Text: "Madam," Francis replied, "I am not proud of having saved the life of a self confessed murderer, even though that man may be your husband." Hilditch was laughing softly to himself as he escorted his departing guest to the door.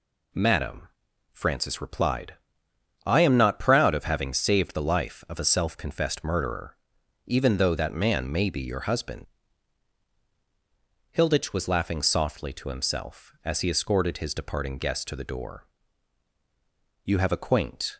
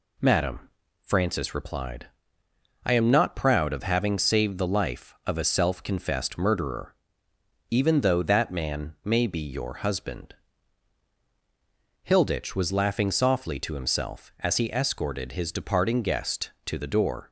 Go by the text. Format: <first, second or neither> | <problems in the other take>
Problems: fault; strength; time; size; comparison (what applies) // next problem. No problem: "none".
second | goes on to say "You have a quaint"; noticeable; from 17.0 s on; 0.94 s long